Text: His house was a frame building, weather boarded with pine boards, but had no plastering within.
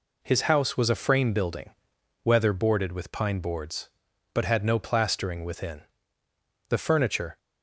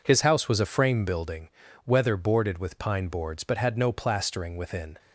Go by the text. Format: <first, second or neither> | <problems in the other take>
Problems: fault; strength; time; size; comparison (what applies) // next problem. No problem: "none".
second | goes on to say "The furniture"; noticeable; from 6.6 s on; 0.68 s long